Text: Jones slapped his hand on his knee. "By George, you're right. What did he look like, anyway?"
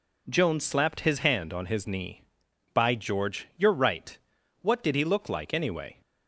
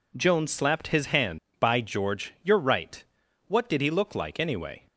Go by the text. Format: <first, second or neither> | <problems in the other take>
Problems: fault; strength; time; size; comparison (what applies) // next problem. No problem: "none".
first | skips "on his knee"; at 1.4 s